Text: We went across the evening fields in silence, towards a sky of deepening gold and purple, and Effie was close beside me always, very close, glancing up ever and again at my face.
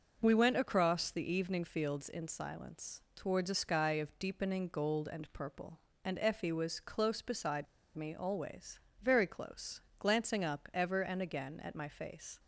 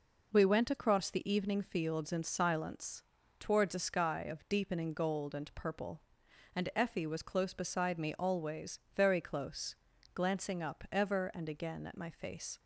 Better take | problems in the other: second | pauses between "beside" and "me"; slight; at 7.6 s; 0.32 s long

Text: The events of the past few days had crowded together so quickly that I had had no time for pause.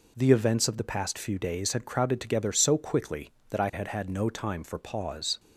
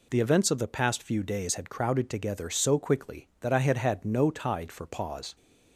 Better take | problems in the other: first | says "tide" for "time"; at 4.3 s

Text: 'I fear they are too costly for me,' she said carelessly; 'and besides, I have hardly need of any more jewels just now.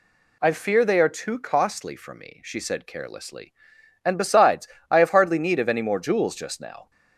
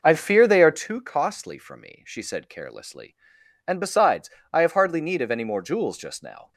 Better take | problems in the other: first | starts louder than the rest; noticeable; until 0.9 s; 5.5 dB

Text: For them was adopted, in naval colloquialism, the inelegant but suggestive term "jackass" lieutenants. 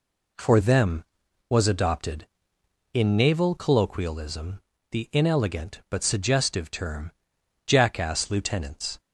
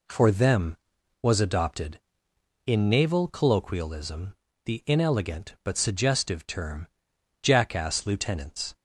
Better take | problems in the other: neither | pauses between "term" and "jackass"; noticeable; the same in both

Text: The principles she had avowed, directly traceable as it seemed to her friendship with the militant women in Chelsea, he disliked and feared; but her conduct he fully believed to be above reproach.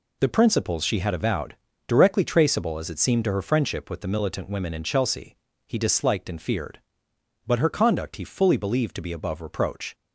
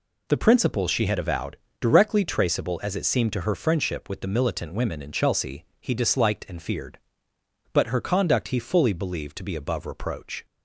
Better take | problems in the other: neither | none

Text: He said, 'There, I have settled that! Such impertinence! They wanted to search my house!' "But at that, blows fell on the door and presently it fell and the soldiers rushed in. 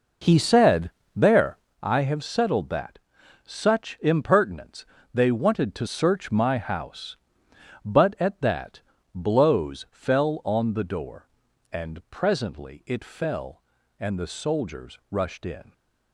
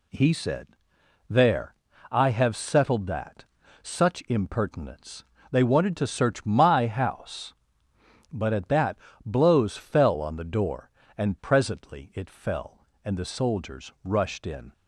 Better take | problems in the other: second | starts louder than the rest; noticeable; until 1.8 s; 5 dB

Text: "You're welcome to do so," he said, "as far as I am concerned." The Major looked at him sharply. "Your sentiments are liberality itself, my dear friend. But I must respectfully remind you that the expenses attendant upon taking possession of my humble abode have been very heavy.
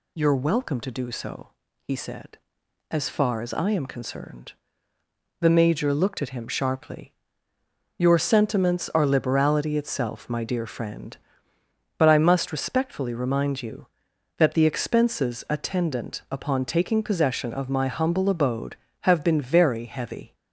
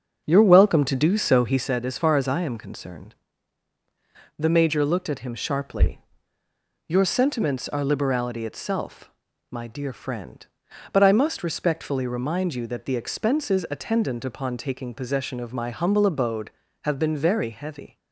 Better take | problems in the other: first | starts louder than the rest; until 1.7 s; 6.5 dB

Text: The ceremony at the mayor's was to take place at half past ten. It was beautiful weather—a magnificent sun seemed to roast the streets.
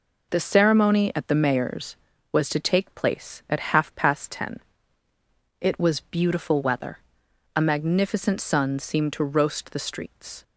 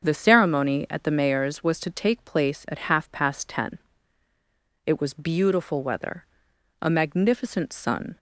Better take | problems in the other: first | starts louder than the rest; until 1.0 s; 7 dB // stops before "seemed to roast the streets"; at 8.1 s

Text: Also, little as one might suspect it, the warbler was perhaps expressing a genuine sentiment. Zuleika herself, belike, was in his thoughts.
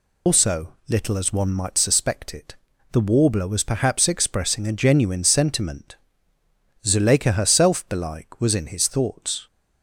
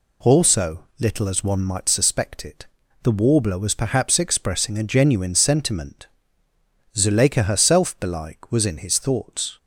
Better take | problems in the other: second | loses the start of "Also"; at 0.2 s; 165 ms

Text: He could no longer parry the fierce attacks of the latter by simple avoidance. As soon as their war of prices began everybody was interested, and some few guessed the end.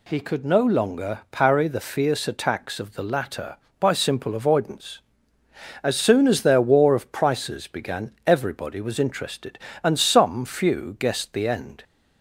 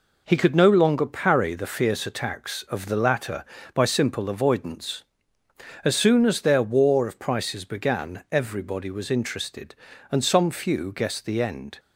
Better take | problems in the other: neither | none

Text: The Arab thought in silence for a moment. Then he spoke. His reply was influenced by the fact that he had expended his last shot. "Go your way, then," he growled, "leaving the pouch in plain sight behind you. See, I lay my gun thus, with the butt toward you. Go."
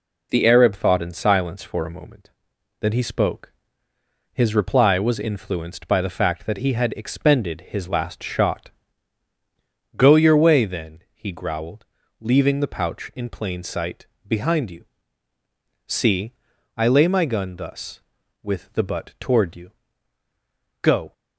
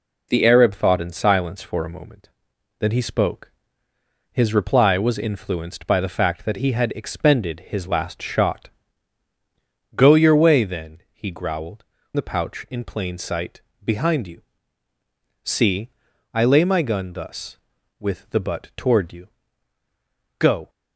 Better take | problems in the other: first | skips "leaving"; at 11.9 s // pauses between "sight" and "behind"; slight; at 13.6 s; 0.22 s long; slight in the first

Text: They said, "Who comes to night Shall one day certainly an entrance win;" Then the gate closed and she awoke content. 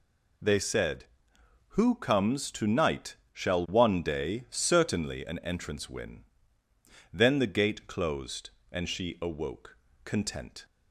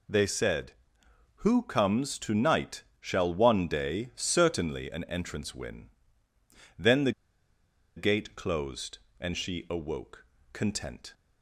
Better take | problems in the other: first | pauses between "night" and "Shall"; slight; at 2.8 s; 0.16 s long; slight in the first // pauses between "the" and "gate"; noticeable; at 7.1 s; 0.85 s long // pauses between "awoke" and "content"; slight; at 10.2 s; 0.30 s long; slight in the first

